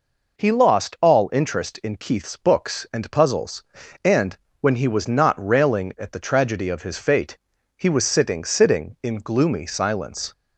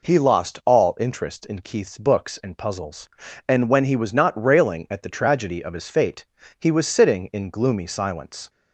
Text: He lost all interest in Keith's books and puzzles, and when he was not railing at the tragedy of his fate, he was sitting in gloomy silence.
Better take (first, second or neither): second